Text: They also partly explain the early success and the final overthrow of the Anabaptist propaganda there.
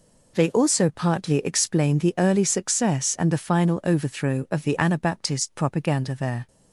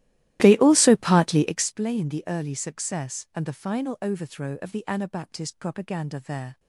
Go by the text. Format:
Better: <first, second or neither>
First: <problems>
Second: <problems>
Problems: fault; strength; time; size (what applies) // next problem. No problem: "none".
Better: first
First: none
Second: starts louder than the rest; strong; until 1.6 s; 15 dB